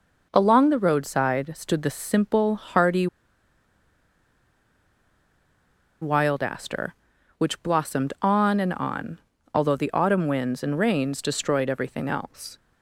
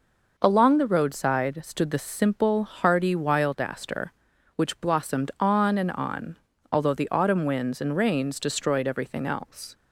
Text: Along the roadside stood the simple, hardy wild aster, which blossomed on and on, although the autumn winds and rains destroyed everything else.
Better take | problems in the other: second | pauses between "hardy" and "wild"; strong; at 3.0 s; 2.9 s long

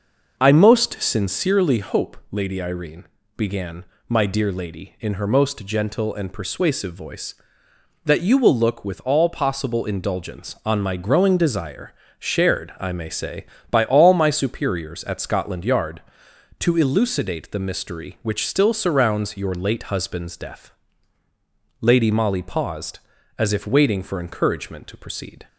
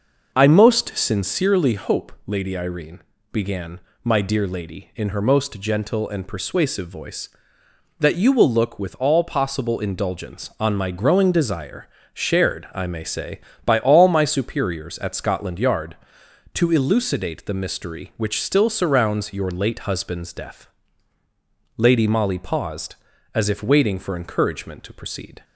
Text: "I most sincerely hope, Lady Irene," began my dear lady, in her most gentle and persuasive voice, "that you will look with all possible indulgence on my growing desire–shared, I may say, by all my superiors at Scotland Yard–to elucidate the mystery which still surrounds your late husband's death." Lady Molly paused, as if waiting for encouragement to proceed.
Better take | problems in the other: neither | pauses between "began" and "my"; slight; the same in both

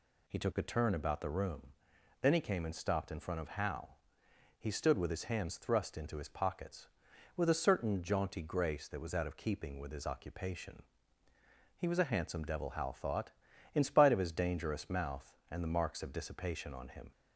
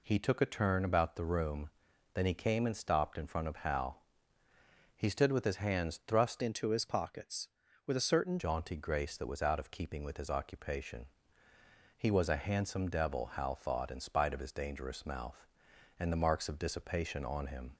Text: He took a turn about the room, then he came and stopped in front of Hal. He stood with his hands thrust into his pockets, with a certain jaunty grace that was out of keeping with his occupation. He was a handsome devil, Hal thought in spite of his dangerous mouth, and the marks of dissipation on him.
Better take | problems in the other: first | changes voice from "into" to "certain"; from 6.4 to 8.3 s; 1.9 s long

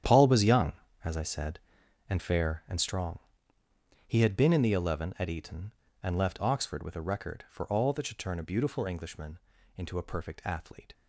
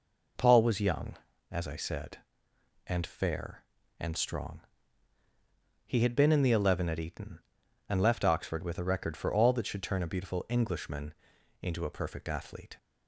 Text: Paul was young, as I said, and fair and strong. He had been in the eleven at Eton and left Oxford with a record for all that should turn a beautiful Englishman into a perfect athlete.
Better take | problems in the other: second | gets quieter; strong; throughout; 14 dB // pauses between "Englishman" and "into"; at 9.3 s; 0.38 s long; noticeable in the second

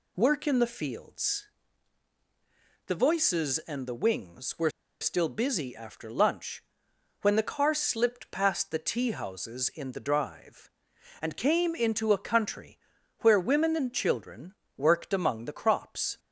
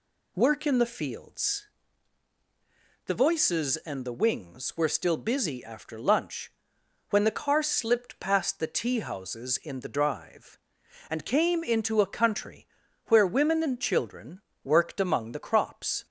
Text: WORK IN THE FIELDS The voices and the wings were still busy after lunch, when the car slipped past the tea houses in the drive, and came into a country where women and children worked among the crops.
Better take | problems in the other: second | pauses between "FIELDS" and "The"; strong; at 1.4 s; 1.3 s long; strong in the second // pauses between "were" and "still"; slight; at 4.6 s; 0.32 s long // pauses between "country" and "where"; noticeable; at 12.7 s; 0.46 s long; also in the second // pauses between "children" and "worked"; slight; at 14.5 s; 0.24 s long; slight in the second

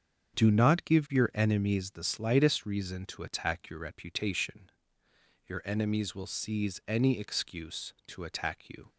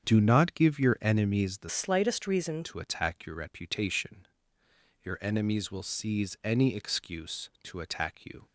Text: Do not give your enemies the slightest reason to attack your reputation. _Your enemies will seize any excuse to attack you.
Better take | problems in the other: first | starts louder than the rest; strong; until 1.0 s; 8 dB; strong in the first // changes voice from "slightest" to "reason"; from 1.6 to 2.6 s; 1.0 s long

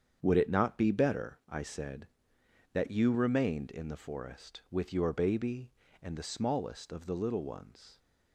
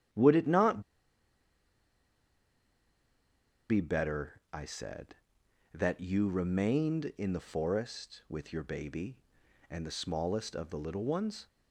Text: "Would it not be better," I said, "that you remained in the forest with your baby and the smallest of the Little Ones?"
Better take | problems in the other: first | starts louder than the rest; strong; until 4.0 s; 10 dB; strong in the first // pauses between "not" and "be"; strong; at 0.8 s; 2.8 s long

